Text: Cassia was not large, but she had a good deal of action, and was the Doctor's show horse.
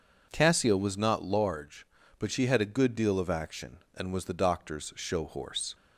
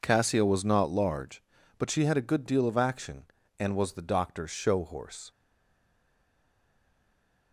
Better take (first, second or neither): first